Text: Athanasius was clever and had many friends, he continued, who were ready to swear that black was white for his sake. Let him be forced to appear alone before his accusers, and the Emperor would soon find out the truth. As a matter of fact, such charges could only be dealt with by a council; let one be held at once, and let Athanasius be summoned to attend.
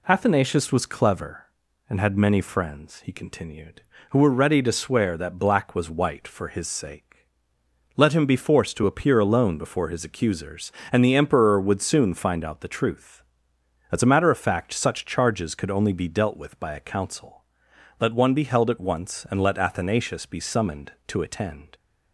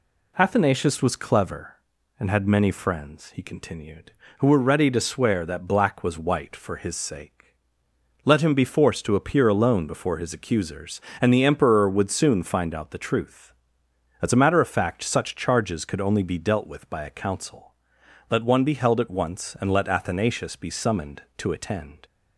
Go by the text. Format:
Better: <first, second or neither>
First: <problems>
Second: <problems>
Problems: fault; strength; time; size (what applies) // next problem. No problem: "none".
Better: neither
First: none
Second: none